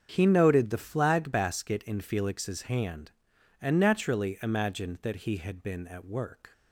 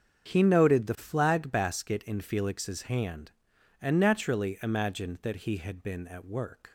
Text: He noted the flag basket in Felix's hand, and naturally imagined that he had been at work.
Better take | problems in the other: neither | starts louder than the rest; strong; the same in both

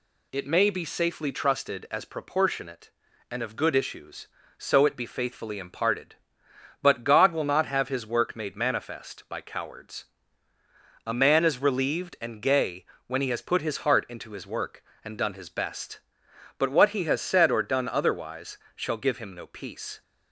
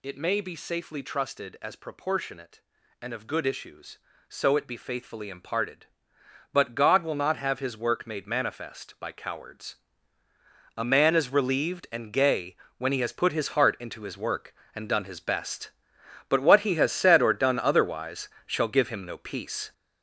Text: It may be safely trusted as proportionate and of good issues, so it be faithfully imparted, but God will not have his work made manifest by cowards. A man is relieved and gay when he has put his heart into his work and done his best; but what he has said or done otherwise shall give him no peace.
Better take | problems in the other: first | gets louder; strong; throughout; 7.5 dB // pauses between "gay" and "when"; slight; at 12.5 s; 0.22 s long; slight in the first // pauses between "otherwise" and "shall"; slight; at 18.2 s; 0.18 s long; slight in the first

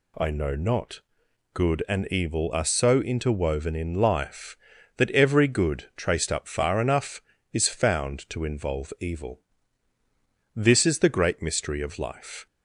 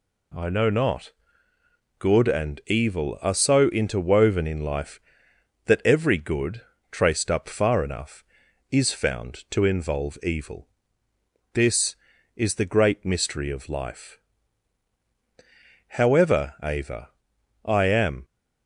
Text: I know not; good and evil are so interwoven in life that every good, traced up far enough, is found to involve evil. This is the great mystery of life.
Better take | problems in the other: first | goes on to say "However Ava I am"; strong; from 15.9 s on; 2.2 s long

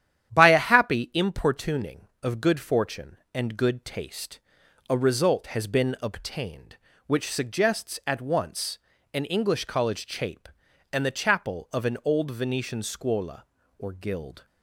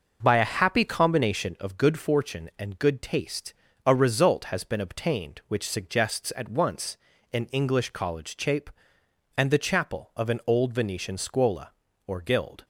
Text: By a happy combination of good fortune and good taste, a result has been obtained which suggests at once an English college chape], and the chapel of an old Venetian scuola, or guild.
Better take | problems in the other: second | starts louder than the rest; strong; until 1.3 s; 10.5 dB // says "importuning" for "combination"; at 1.1 s // pauses between "once" and "an"; slight; at 8.7 s; 0.34 s long; also in the second

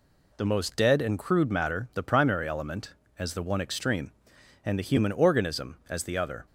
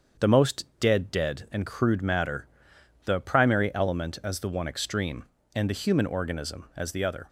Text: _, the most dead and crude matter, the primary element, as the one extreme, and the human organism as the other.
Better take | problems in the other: first | starts louder than the rest; until 1.3 s; 7 dB // says "dead" twice; at 1.1 s

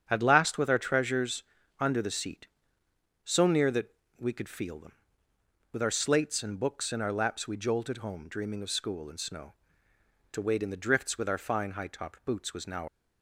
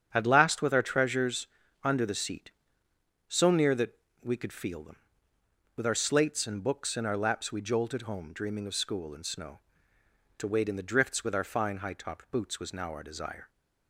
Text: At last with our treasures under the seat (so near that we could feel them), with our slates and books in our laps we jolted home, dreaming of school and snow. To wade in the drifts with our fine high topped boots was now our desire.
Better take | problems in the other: second | starts louder than the rest; strong; until 1.0 s; 8 dB; strong in the second // pauses between "treasures" and "under"; at 1.4 s; 0.38 s long; also in the second // pauses between "that" and "we"; slight; at 3.9 s; 0.24 s long; slight in the second // stops before "our desire"; at 12.8 s

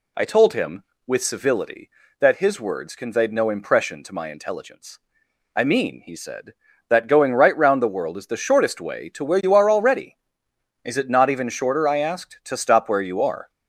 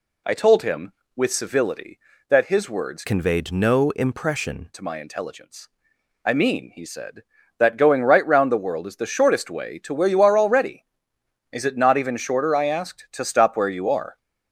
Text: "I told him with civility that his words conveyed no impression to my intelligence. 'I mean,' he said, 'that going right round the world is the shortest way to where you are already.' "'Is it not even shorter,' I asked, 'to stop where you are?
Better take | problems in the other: first | changes voice from "conveyed" to "impression"; from 3.0 to 4.6 s; 1.6 s long

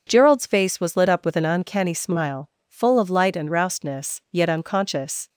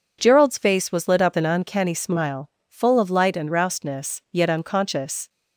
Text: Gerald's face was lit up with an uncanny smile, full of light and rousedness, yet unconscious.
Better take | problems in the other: first | skips "with"; at 1.3 s

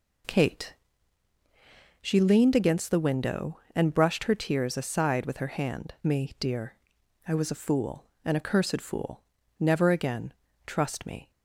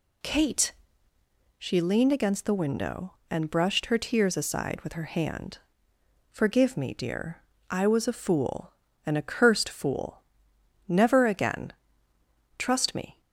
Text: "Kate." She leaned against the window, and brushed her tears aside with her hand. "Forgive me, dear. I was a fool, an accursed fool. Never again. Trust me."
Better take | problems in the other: second | skips "Forgive"; at 5.9 s

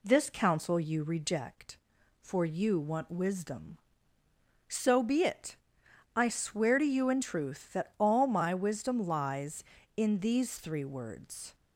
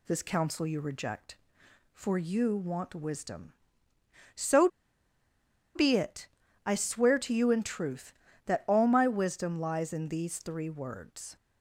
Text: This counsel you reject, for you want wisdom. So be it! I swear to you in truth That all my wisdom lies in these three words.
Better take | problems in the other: first | pauses between "So" and "be"; at 4.6 s; 1.0 s long

